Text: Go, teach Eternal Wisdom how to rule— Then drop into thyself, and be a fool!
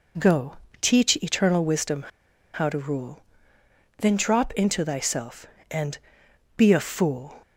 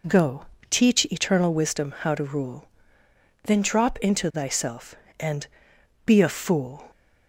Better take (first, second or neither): second